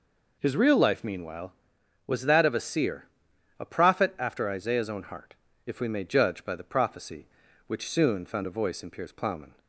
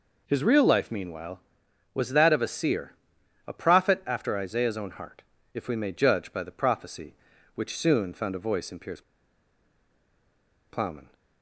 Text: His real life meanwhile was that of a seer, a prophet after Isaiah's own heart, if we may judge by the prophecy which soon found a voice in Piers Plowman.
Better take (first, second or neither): first